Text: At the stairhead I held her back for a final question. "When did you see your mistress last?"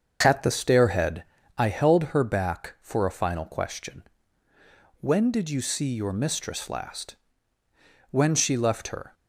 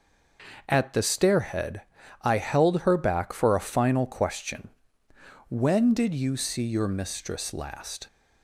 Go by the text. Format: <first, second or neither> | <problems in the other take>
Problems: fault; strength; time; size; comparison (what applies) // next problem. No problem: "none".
second | starts louder than the rest; until 1.2 s; 6.5 dB // pauses between "stairhead" and "I"; slight; at 1.2 s; 0.34 s long; also in the second // goes on to say "When she left her"; noticeable; from 8.1 s on; 1.0 s long